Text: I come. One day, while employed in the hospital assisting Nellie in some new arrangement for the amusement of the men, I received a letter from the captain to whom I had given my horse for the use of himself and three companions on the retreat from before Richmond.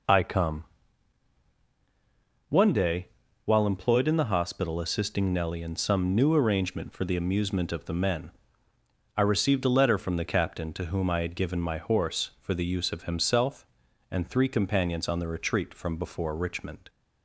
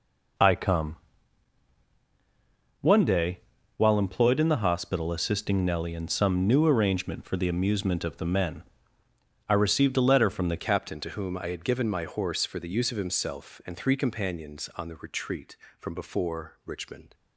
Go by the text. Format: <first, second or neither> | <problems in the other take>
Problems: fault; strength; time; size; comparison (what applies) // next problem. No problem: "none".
first | changes voice at "captain"; from 10.5 s on; 6.6 s long